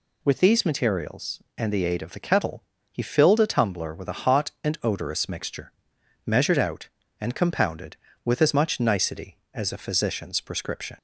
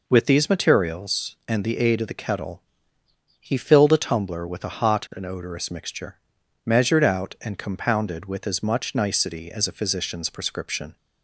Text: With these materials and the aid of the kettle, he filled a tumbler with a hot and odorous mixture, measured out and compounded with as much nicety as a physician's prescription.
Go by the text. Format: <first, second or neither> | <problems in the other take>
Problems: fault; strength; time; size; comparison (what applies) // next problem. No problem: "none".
neither | none